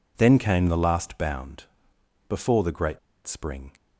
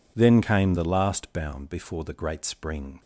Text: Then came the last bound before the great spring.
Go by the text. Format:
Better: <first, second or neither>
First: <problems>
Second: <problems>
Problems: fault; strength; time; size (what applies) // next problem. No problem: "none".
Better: second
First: pauses between "bound" and "before"; noticeable; at 1.6 s; 0.64 s long // pauses between "great" and "spring"; slight; at 2.9 s; 0.27 s long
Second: none